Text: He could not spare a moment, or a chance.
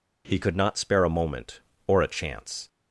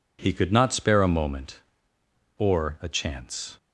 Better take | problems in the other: second | changes voice at "could"; from 0.4 s on; 2.2 s long

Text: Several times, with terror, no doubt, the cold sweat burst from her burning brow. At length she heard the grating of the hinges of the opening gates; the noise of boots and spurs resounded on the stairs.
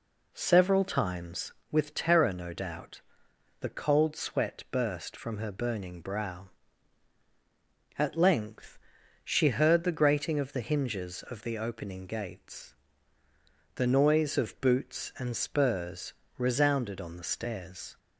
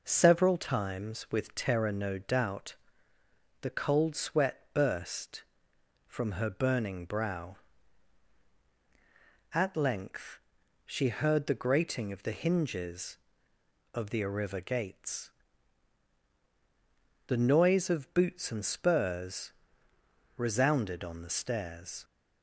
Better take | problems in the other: first | pauses between "length" and "she"; at 10.3 s; 0.44 s long; noticeable in the first // says "arriva" for "opening"; at 14.1 s // pauses between "spurs" and "resounded"; noticeable; at 19.5 s; 0.82 s long; slight in the first

